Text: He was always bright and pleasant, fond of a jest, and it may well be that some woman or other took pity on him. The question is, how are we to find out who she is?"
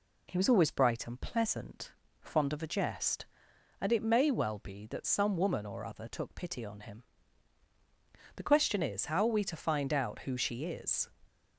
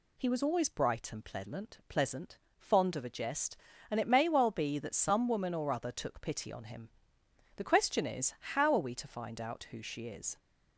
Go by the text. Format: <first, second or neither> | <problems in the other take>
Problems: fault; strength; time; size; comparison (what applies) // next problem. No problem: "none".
first | says "pleasant" twice; at 1.8 s